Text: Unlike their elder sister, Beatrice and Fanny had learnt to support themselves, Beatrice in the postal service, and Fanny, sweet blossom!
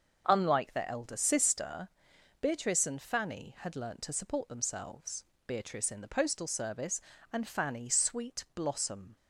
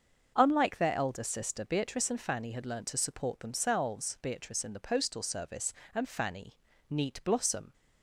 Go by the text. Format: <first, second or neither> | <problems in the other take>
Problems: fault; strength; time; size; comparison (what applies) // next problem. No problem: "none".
first | starts louder than the rest; until 1.3 s; 6.5 dB; also in the first // says "neat" for "sweet"; at 6.8 s